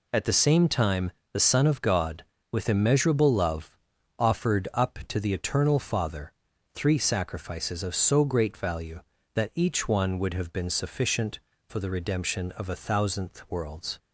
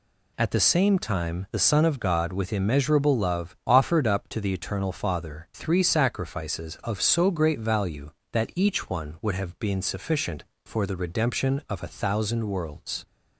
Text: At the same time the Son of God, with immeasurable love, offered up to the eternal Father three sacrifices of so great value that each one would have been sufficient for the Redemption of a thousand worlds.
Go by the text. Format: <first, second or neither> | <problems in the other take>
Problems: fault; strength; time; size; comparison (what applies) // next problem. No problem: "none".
second | pauses between "time" and "the"; slight; at 1.1 s; 0.22 s long // pauses between "Father" and "three"; at 6.3 s; 0.42 s long // says "thousandth" for "thousand"; at 12.7 s